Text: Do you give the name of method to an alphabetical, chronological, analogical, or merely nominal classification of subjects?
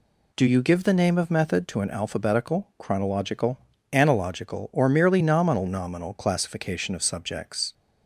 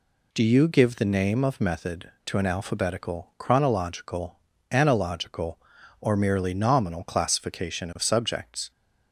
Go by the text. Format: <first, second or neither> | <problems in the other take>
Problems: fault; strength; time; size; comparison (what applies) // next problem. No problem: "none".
second | says "nominal" twice; at 5.6 s